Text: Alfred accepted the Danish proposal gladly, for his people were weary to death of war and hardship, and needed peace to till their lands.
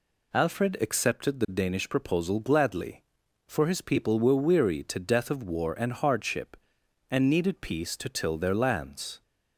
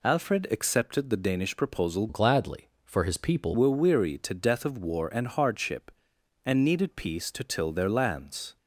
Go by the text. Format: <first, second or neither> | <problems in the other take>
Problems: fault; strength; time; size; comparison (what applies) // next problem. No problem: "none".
first | changes voice from "gladly" to "people"; from 2.0 to 3.5 s; 1.5 s long